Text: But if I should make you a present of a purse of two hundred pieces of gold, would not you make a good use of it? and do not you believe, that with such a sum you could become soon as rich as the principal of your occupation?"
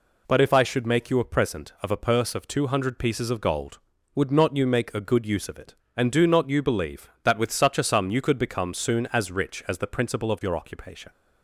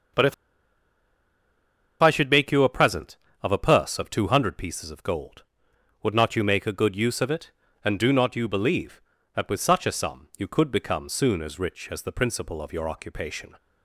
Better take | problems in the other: first | starts louder than the rest; until 2.8 s; 6.5 dB // pauses between "if" and "I"; strong; at 0.3 s; 1.6 s long

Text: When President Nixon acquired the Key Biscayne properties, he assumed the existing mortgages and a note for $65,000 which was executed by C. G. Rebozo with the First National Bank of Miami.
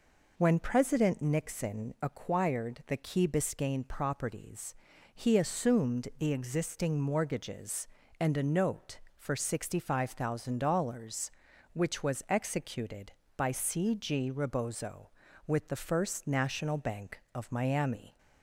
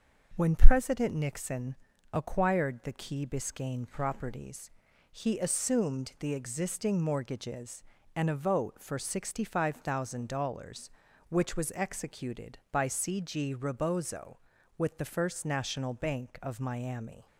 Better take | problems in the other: first | pauses between "Nixon" and "acquired"; slight; at 1.7 s; 0.36 s long // says "vote" for "note"; at 8.3 s

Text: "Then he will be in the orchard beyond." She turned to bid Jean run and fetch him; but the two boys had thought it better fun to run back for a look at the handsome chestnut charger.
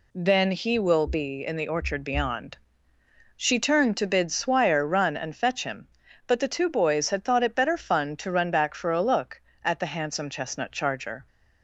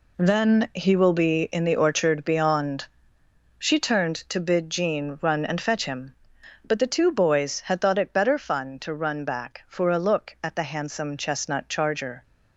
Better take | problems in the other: second | says "Swire" for "Jean"; at 4.3 s

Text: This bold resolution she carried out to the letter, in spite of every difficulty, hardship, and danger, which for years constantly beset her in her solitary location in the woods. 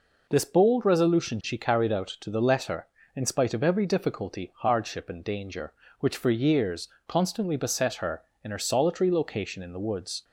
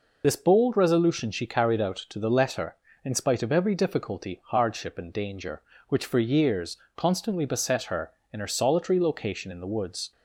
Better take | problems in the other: first | loses the start of "This"; at 0.2 s; 40 ms // pauses between "years" and "constantly"; slight; at 6.7 s; 0.18 s long; slight in the first

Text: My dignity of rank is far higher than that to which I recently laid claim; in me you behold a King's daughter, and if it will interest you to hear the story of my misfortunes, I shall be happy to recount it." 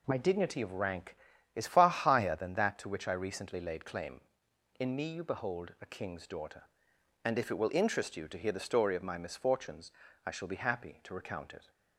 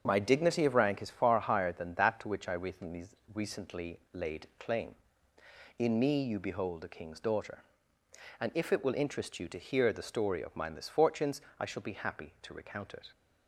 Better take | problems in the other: first | starts louder than the rest; strong; until 1.0 s; 7 dB // says "recently" twice; at 3.3 s

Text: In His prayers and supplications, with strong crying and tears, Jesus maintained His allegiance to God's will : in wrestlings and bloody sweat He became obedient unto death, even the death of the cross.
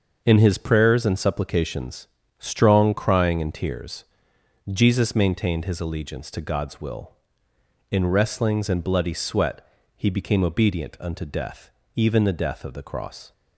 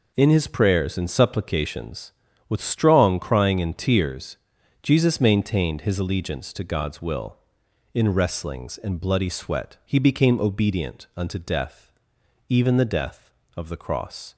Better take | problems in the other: second | starts louder than the rest; until 1.2 s; 6.5 dB // skips "with"; at 2.2 s // pauses between "sweat" and "He"; slight; at 9.6 s; 0.30 s long

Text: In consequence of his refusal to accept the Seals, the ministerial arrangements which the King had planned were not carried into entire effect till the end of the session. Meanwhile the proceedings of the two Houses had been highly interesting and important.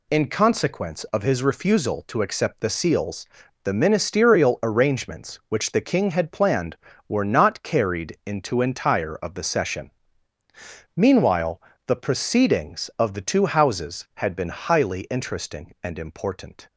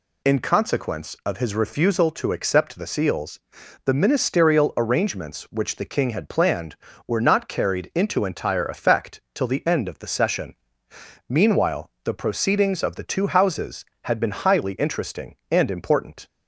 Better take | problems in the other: second | skips "effect till the end"; at 9.1 s // pauses between "Meanwhile" and "the"; slight; at 11.5 s; 0.28 s long

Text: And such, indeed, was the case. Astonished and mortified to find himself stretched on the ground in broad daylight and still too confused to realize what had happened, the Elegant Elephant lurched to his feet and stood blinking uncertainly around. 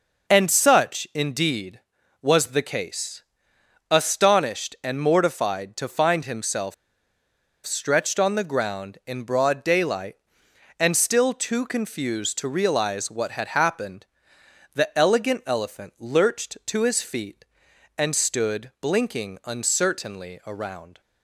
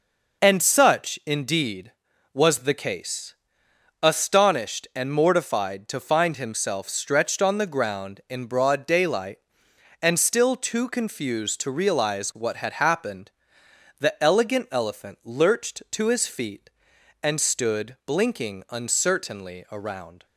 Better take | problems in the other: second | pauses between "himself" and "stretched"; noticeable; at 6.7 s; 0.91 s long

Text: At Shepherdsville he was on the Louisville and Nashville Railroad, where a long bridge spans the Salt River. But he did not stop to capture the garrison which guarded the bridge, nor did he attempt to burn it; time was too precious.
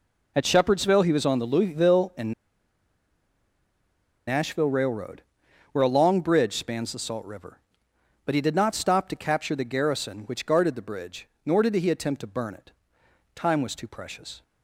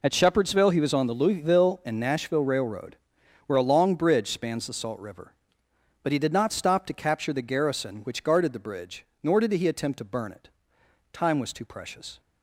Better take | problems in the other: second | pauses between "and" and "Nashville"; strong; at 2.3 s; 1.9 s long

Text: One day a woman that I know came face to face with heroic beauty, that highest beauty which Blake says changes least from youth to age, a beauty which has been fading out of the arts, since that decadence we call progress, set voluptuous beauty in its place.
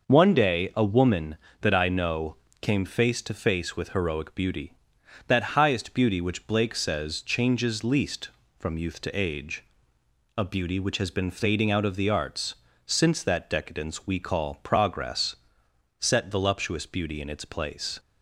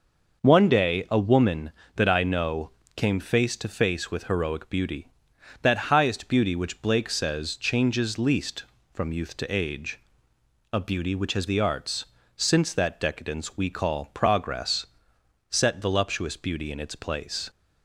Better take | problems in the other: first | pauses between "know" and "came"; slight; at 2.7 s; 0.24 s long; slight in the first // skips "been fading out of"; at 11.4 s

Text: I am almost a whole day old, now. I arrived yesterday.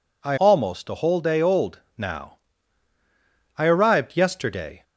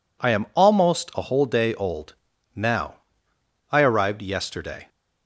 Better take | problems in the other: second | skips "am"; at 0.3 s

